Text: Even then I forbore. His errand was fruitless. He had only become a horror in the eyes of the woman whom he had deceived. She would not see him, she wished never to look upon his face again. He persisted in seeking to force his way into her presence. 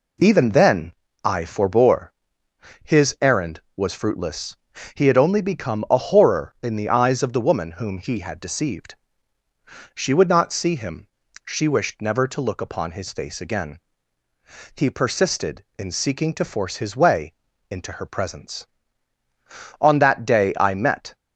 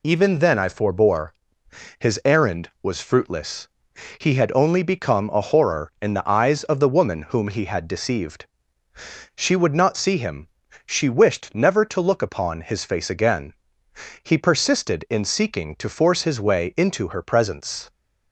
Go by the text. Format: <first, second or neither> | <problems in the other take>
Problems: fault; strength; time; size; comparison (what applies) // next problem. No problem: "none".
second | pauses between "then" and "I"; slight; at 0.9 s; 0.32 s long // pauses between "way" and "into"; at 17.3 s; 0.38 s long // goes on to say "On that day I met"; from 19.7 s on; 1.3 s long